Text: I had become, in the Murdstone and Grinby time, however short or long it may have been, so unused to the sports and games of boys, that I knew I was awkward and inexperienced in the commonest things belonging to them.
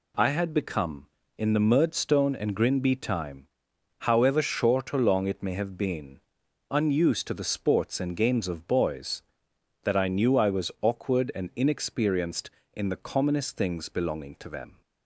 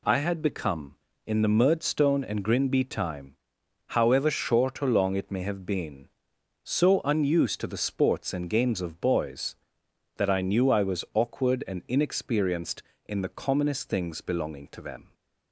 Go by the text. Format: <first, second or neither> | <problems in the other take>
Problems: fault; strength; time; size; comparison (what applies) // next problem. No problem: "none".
second | skips "so"; at 6.4 s